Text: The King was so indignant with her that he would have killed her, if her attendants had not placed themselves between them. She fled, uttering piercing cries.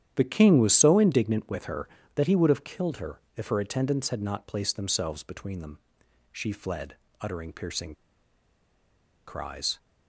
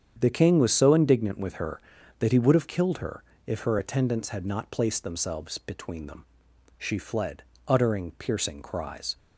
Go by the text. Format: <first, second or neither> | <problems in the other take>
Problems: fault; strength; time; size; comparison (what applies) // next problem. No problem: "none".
second | starts louder than the rest; strong; until 1.1 s; 10 dB; strong in the second // pauses between "piercing" and "cries"; strong; at 7.9 s; 1.3 s long